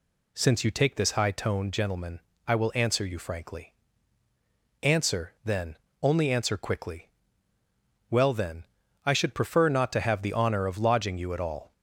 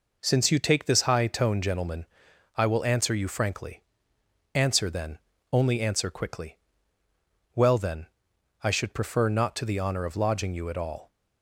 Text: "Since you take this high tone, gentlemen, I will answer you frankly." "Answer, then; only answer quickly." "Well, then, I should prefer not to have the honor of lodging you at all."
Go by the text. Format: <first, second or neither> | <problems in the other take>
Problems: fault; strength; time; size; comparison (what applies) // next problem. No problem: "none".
first | skips "have"; at 9.6 s